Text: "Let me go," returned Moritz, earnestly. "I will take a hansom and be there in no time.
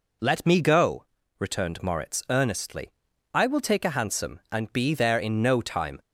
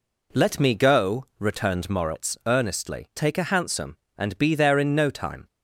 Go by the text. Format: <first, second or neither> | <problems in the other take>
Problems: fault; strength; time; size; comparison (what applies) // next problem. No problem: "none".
first | skips "I will"; at 3.1 s